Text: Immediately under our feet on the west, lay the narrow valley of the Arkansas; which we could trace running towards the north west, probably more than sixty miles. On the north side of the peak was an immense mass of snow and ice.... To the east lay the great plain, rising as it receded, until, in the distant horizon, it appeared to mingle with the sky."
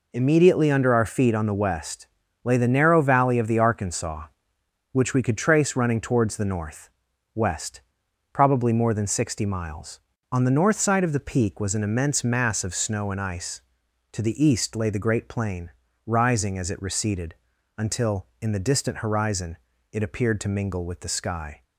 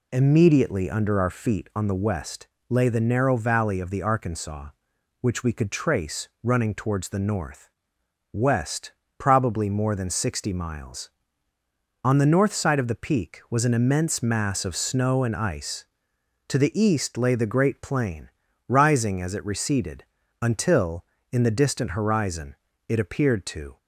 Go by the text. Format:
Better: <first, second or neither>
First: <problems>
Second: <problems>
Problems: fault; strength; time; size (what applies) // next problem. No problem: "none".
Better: first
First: pauses between "north" and "west"; noticeable; at 6.8 s; 0.46 s long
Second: pauses between "north" and "west"; noticeable; at 7.6 s; 0.62 s long // stops before "mingle with the sky"; at 23.7 s